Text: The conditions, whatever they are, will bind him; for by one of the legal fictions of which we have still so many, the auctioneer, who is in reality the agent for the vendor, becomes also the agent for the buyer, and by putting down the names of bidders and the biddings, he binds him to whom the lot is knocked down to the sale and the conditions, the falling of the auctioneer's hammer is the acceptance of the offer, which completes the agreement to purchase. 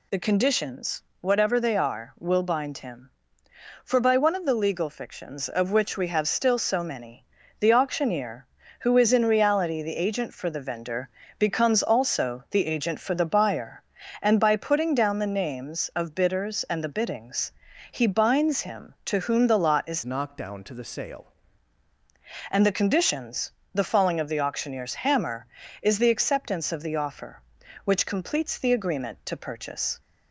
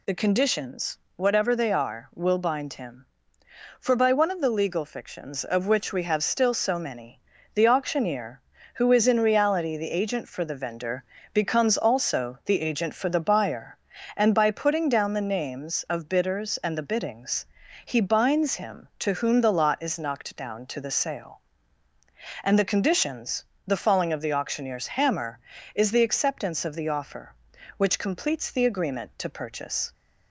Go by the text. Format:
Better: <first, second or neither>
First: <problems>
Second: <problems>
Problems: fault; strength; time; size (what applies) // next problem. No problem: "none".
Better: second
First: changes voice from "knocked" to "sale"; from 20.0 to 21.3 s; 1.3 s long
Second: none